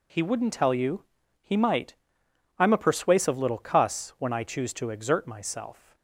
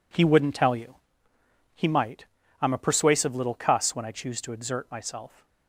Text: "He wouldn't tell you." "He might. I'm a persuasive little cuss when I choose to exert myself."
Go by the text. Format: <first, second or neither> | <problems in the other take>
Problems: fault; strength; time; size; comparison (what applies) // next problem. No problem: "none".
neither | none